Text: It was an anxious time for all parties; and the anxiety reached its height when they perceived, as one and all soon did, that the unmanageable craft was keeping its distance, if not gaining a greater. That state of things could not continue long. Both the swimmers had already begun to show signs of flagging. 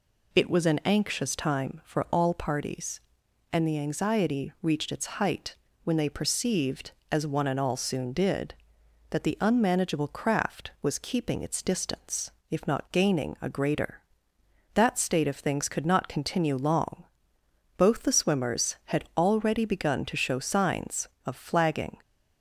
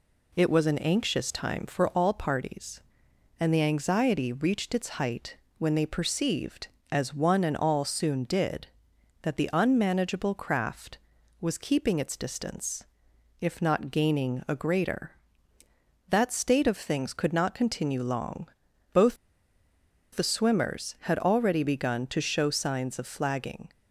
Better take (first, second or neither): first